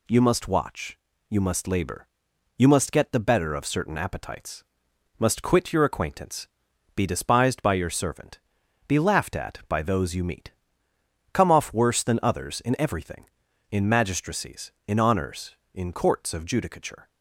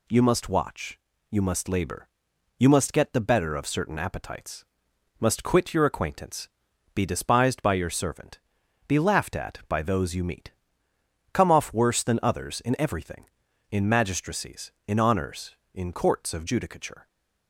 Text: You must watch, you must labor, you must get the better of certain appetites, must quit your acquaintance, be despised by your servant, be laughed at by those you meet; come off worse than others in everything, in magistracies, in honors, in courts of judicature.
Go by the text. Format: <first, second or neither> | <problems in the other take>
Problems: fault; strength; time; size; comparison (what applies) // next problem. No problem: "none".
neither | none